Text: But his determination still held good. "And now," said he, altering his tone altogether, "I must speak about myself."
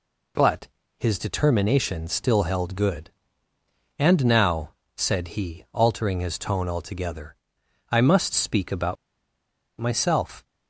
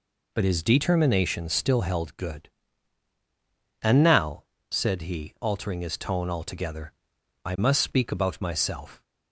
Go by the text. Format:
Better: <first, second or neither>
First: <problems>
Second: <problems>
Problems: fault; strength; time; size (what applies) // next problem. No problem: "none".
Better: second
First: pauses between "But" and "his"; slight; at 0.6 s; 0.30 s long // pauses between "about" and "myself"; noticeable; at 8.9 s; 0.85 s long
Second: none